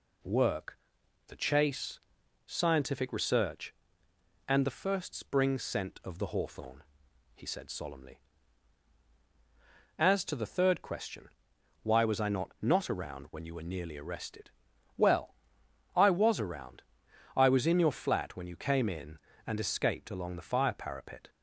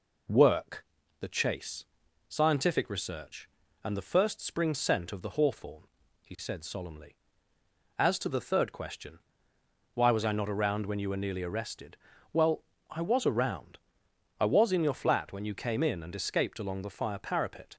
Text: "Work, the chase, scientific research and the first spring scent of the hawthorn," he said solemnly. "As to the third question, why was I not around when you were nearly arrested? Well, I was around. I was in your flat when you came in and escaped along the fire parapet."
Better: second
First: says "not" twice; at 12.6 s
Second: none

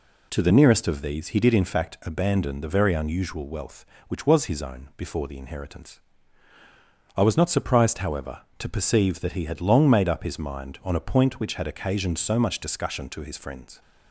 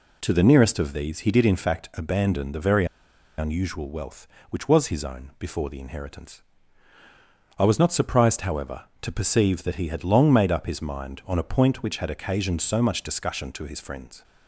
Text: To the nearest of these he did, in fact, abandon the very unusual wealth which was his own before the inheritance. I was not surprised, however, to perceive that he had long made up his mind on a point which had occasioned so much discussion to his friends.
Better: first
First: none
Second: pauses between "very" and "unusual"; noticeable; at 2.8 s; 0.53 s long

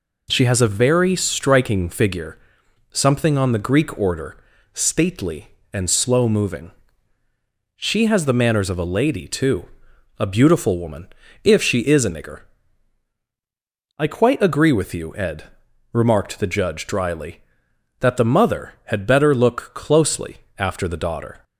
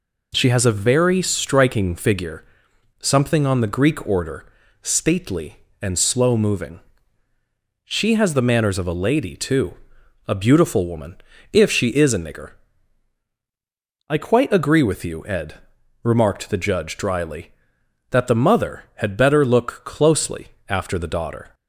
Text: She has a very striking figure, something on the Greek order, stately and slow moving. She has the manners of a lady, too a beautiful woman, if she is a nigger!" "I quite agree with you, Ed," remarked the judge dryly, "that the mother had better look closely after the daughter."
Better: neither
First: pauses between "too" and "a"; noticeable; at 9.6 s; 0.54 s long // pauses between "closely" and "after"; slight; at 20.3 s; 0.20 s long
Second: pauses between "too" and "a"; noticeable; at 9.7 s; 0.54 s long // pauses between "closely" and "after"; slight; at 20.4 s; 0.20 s long

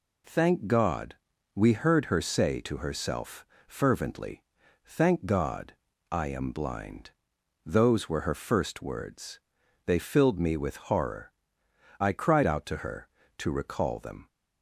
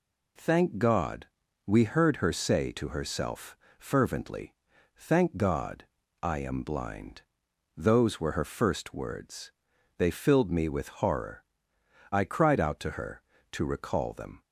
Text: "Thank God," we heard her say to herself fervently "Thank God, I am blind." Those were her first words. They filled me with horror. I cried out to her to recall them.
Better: neither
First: pauses between "herself" and "fervently"; slight; at 3.4 s; 0.22 s long // pauses between "fervently" and "Thank"; at 4.4 s; 0.42 s long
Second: pauses between "herself" and "fervently"; slight; at 3.5 s; 0.22 s long // pauses between "fervently" and "Thank"; at 4.5 s; 0.42 s long

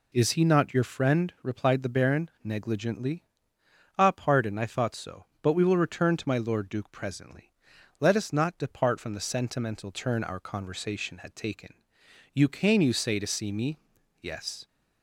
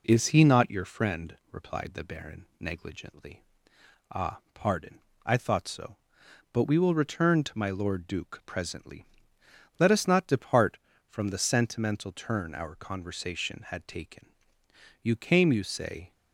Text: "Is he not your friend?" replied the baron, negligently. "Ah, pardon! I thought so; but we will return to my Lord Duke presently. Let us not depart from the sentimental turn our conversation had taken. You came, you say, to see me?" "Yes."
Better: first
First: none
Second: stops before "to see me Yes"; at 16.1 s

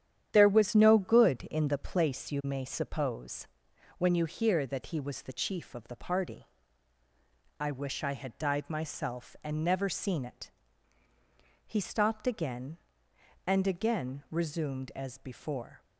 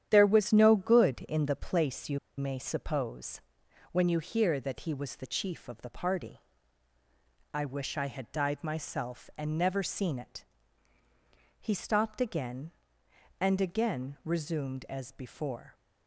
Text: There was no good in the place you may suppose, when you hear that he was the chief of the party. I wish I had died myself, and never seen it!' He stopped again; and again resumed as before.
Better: first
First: starts louder than the rest; strong; until 1.3 s; 10 dB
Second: starts louder than the rest; strong; until 1.1 s; 10 dB // pauses between "you" and "may"; slight; at 2.1 s; 0.19 s long

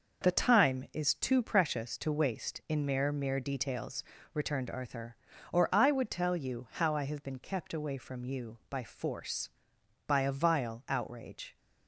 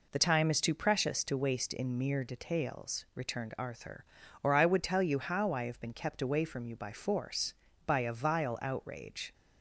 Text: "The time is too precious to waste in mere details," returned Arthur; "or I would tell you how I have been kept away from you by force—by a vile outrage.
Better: second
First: says "mere" twice; at 3.1 s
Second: none

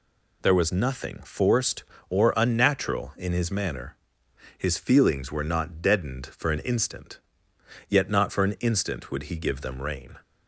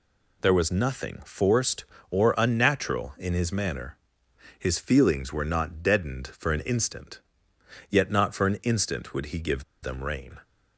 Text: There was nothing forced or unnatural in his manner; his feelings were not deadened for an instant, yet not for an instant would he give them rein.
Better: first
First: none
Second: pauses between "give" and "them"; slight; at 9.6 s; 0.19 s long

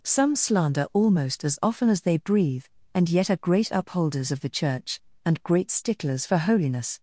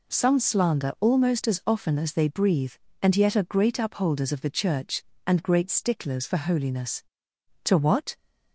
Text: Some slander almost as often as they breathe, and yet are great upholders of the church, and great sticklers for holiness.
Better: first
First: none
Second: goes on to say "To what"; from 7.6 s on; 0.52 s long

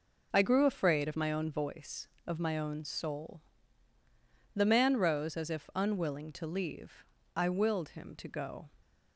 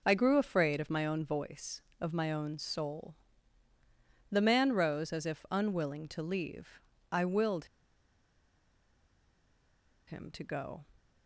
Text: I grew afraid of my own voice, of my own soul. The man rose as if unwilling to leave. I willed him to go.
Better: first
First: none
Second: pauses between "willed" and "him"; strong; at 7.6 s; 2.4 s long

